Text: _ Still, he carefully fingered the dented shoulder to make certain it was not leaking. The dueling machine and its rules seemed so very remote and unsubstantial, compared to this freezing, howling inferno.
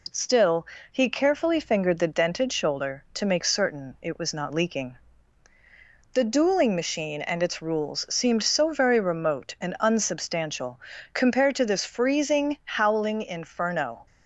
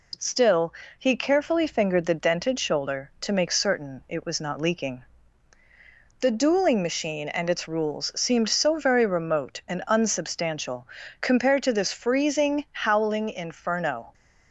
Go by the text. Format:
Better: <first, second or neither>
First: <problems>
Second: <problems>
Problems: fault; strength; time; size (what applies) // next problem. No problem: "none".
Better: neither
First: none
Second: none